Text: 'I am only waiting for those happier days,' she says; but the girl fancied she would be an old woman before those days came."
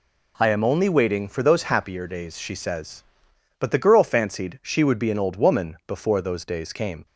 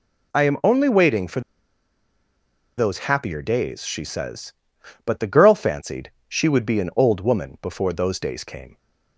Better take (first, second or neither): first